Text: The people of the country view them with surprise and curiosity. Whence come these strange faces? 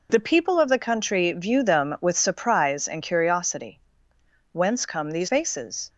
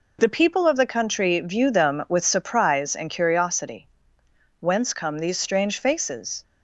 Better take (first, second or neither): second